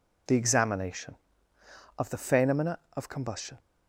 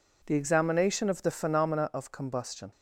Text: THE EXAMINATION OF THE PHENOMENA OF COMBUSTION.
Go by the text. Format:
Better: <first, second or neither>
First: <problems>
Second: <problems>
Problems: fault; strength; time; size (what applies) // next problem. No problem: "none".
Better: neither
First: none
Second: none